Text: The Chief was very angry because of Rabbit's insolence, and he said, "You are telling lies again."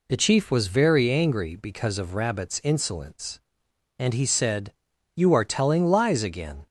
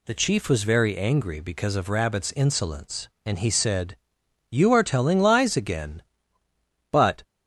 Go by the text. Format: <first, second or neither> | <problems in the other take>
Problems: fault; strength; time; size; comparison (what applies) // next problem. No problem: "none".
first | goes on to say "But"; slight; from 6.9 s on; 0.30 s long